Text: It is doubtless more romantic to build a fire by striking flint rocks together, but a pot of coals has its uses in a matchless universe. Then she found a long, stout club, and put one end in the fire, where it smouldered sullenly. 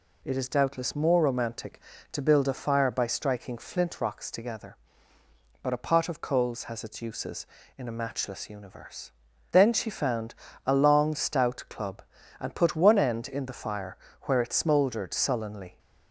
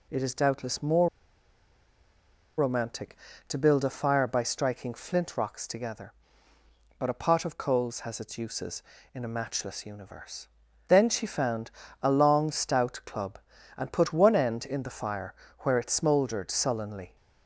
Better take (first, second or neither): first